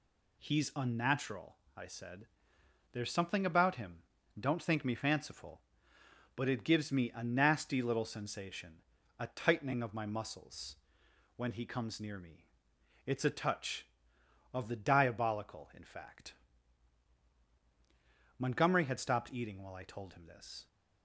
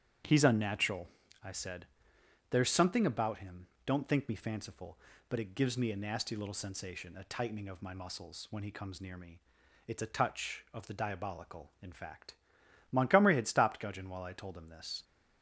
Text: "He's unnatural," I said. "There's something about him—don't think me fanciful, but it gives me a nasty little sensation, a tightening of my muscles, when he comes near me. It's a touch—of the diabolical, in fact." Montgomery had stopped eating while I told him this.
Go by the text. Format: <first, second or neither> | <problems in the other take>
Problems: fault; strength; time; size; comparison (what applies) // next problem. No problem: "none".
first | starts louder than the rest; strong; until 1.6 s; 9 dB // says "gudgeon" for "eating"; at 13.7 s